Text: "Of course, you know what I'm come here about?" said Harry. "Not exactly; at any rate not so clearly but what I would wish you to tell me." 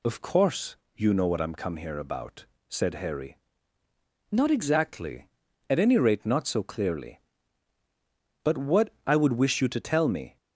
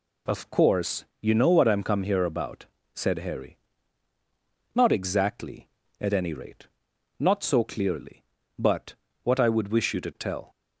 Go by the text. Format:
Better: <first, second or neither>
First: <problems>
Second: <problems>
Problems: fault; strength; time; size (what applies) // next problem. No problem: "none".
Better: first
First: none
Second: pauses between "rate" and "not"; noticeable; at 6.6 s; 0.50 s long // pauses between "but" and "what"; slight; at 8.9 s; 0.28 s long // stops before "me"; at 10.5 s